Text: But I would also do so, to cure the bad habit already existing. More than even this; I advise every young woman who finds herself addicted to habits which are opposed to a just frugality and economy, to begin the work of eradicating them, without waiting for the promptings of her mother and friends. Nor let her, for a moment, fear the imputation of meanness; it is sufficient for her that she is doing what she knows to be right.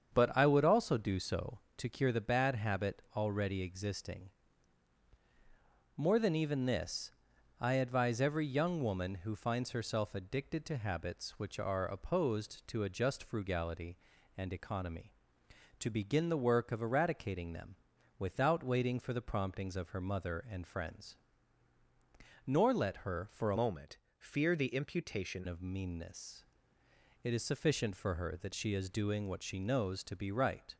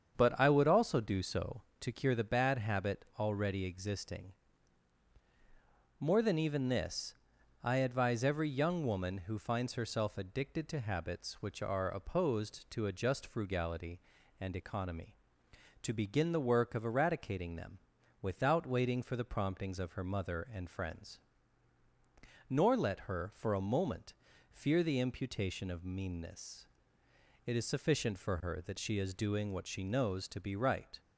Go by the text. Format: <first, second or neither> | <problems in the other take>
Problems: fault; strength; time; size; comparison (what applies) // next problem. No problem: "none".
second | starts louder than the rest; strong; until 1.1 s; 7.5 dB; strong in the second // changes voice from "moment" to "imputation"; from 23.5 to 25.4 s; 1.9 s long